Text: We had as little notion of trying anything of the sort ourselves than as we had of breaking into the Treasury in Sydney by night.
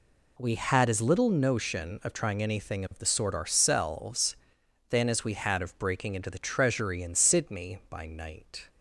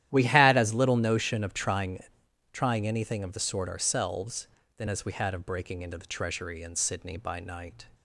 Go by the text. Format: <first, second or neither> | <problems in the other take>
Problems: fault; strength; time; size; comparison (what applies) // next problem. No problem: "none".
first | starts louder than the rest; strong; until 1.1 s; 12.5 dB // says "trying" twice; at 2.5 s